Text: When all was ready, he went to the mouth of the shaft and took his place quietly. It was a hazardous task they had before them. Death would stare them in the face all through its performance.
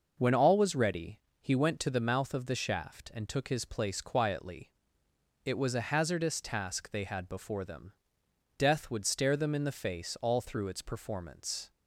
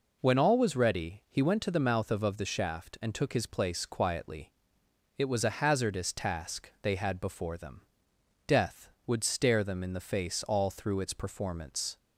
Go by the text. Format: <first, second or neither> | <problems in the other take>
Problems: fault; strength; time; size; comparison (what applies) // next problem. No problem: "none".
first | says "of" twice; at 2.2 s